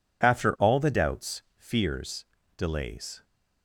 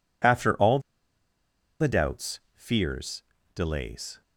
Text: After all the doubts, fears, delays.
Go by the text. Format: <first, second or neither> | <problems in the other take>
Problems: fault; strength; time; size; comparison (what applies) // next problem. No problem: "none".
first | pauses between "all" and "the"; at 0.7 s; 1.0 s long